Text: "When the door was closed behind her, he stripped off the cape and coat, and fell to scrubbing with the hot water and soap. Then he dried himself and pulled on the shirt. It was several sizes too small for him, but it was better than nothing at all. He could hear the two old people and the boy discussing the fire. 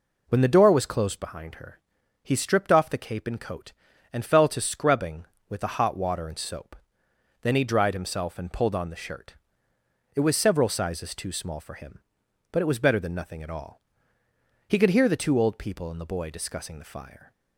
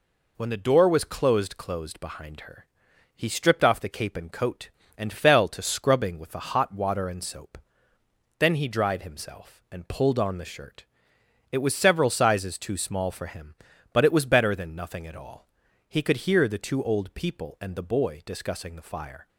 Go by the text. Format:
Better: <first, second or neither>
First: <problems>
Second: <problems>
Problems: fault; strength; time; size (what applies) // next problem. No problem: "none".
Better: first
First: none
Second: says "closed" twice; at 1.5 s